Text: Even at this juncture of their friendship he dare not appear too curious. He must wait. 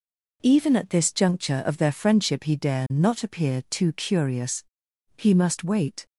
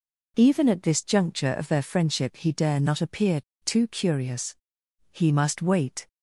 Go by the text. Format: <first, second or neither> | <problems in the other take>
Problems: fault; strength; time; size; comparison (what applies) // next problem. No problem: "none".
first | pauses between "appear" and "too"; slight; at 3.4 s; 0.23 s long